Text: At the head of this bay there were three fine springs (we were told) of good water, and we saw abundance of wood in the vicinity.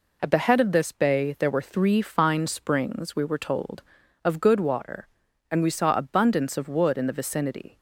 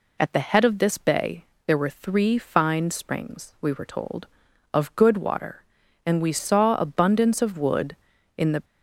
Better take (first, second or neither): first